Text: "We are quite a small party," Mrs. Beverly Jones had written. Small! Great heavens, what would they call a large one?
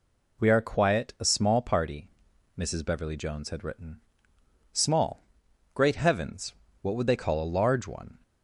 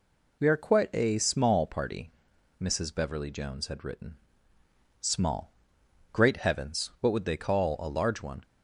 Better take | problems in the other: second | says "quiet" for "quite"; at 0.6 s

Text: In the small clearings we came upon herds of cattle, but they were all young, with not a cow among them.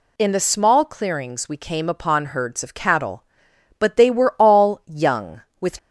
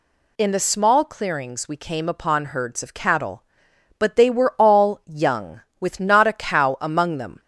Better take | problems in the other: second | stops before "not a cow among them"; at 5.7 s

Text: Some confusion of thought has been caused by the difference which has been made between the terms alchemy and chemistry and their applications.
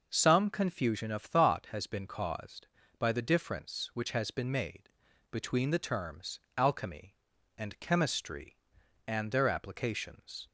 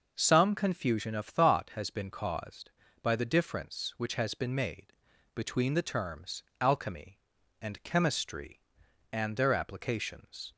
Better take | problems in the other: neither | pauses between "made" and "between"; the same in both // pauses between "terms" and "alchemy"; slight; the same in both

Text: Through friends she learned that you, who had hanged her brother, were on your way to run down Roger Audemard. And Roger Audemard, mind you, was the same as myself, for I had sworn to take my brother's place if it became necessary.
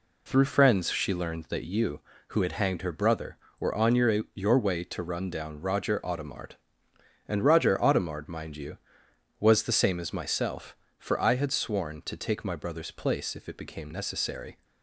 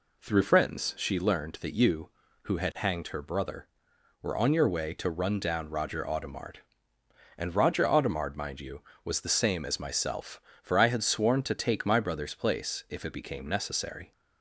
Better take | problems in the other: second | says "your" twice; at 4.3 s

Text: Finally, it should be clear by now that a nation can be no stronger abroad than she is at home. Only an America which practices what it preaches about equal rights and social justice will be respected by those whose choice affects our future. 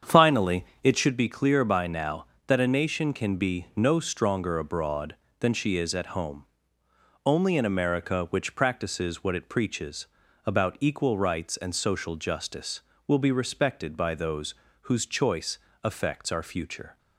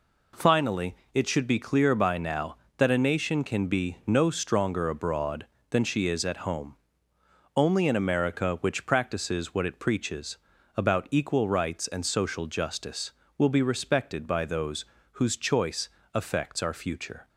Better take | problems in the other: second | starts louder than the rest; strong; until 1.1 s; 8 dB // pauses between "preaches" and "about"; at 10.0 s; 0.40 s long; also in the second // pauses between "those" and "whose"; slight; at 14.5 s; 0.28 s long; slight in the second // pauses between "choice" and "affects"; slight; at 15.5 s; 0.26 s long; slight in the second

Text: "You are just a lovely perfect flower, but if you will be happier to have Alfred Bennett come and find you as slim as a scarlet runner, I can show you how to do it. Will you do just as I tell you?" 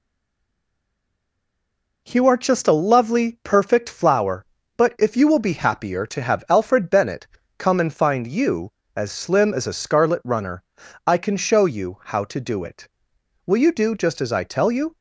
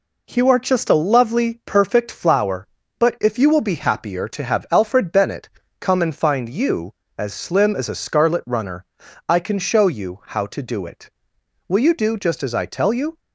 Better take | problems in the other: second | stays silent before the first word; noticeable; until 2.0 s; 2.0 s long // pauses between "Bennett" and "come"; slight; at 7.2 s; 0.30 s long; slight in the second

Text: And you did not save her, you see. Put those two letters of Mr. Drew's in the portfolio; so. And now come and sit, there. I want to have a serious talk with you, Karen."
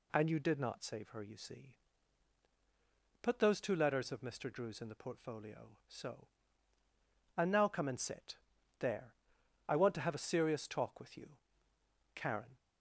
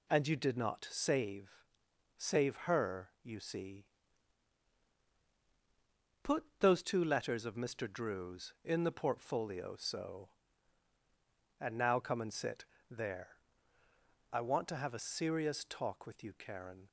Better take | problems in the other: first | says "save" twice; at 2.1 s // pauses between "Put" and "those"; slight; at 6.4 s; 0.16 s long

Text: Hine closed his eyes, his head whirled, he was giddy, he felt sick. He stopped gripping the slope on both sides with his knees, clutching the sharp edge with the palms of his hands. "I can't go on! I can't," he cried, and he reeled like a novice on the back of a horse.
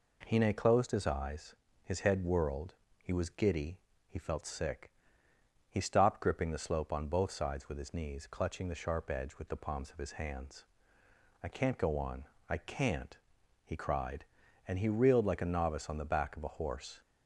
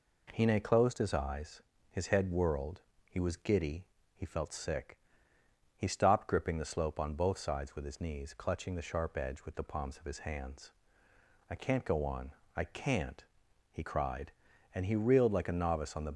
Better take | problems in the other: first | stops before "back of a horse"; at 16.1 s

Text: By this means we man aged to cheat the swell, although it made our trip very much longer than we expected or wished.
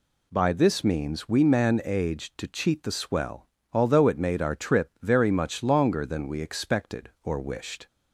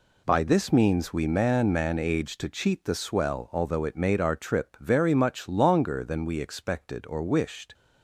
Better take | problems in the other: first | says "man" twice; at 1.7 s

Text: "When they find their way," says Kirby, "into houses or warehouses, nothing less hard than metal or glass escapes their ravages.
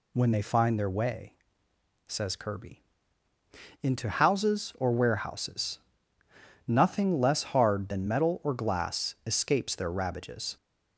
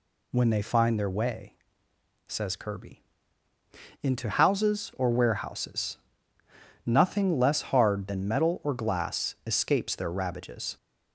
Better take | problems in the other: neither | none

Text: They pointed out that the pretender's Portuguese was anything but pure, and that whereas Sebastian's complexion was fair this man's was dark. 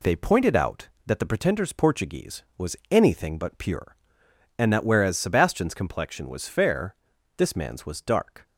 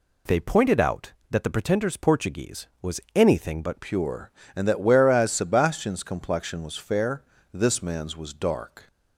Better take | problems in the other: first | changes voice at "pure"; from 3.8 s on; 5.0 s long // pauses between "fair" and "this"; slight; at 7.2 s; 0.32 s long; also in the first

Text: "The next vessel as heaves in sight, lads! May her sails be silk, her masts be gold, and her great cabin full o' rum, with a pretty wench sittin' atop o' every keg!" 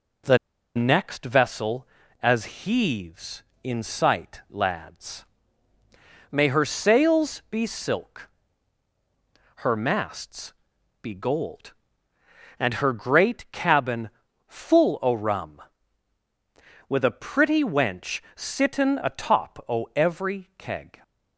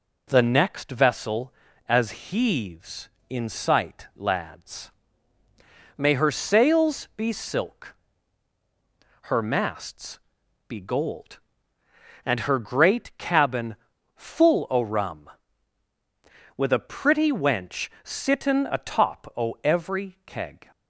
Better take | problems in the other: second | pauses between "The" and "next"; at 0.3 s; 0.38 s long // pauses between "masts" and "be"; noticeable; at 10.5 s; 0.50 s long; noticeable in the second // pauses between "cabin" and "full"; at 14.0 s; 0.38 s long; also in the second // pauses between "wench" and "sittin"; slight; at 18.2 s; 0.16 s long; slight in the second

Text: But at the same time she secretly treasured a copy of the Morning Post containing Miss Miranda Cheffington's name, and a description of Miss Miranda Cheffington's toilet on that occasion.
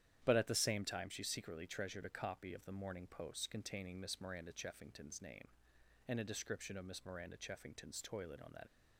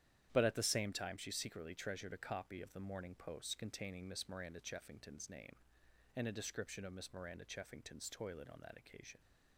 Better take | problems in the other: second | starts louder than the rest; strong; until 1.2 s; 10.5 dB; strong in the second // stops before "occasion"; at 8.6 s

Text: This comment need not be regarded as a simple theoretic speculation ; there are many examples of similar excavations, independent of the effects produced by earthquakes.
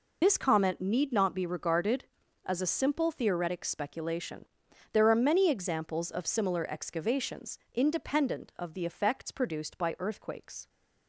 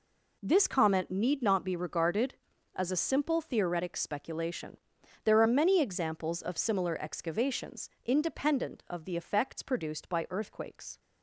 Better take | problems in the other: second | loses the start of "This"; at 0.2 s; 110 ms

